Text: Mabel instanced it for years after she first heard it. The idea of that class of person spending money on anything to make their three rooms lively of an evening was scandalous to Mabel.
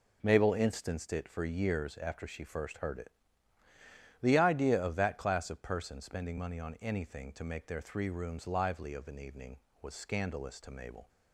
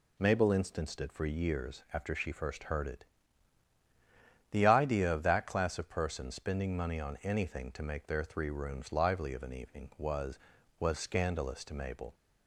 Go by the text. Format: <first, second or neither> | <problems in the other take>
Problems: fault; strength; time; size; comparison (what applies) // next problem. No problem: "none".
first | says "was" twice; at 10.7 s